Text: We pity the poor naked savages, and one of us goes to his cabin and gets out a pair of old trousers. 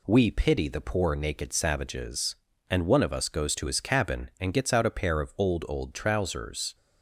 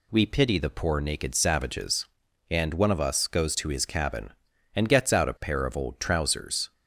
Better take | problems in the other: second | says "old" twice; at 5.6 s

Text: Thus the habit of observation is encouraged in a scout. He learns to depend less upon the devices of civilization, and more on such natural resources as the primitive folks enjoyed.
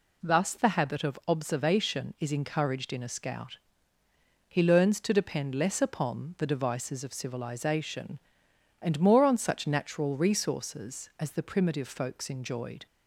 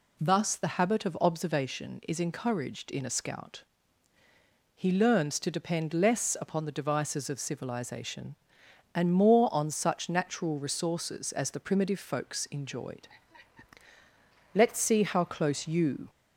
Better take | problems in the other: first | goes on to say "Let's see how close you"; from 14.5 s on; 1.5 s long

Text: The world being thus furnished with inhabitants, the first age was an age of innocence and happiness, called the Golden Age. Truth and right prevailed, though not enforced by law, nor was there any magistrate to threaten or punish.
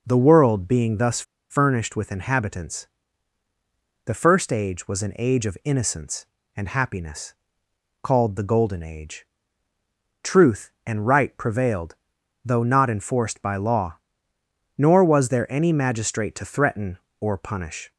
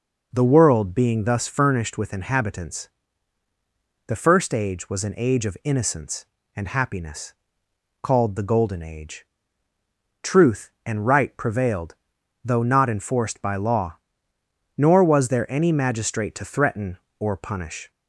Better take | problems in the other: second | pauses between "thus" and "furnished"; slight; at 1.2 s; 0.28 s long

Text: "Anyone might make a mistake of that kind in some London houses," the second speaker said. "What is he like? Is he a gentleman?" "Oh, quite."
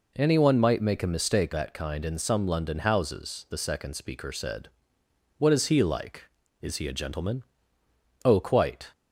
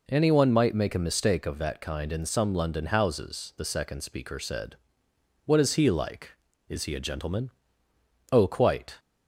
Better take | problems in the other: second | skips "of"; at 1.5 s

